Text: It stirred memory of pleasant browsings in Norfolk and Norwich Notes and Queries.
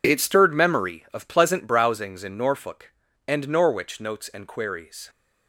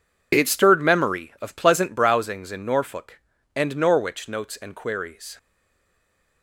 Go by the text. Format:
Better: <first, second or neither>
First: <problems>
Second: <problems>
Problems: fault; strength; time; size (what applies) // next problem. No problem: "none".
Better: first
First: none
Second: stays silent after the last word; from 5.3 s on; 1.1 s long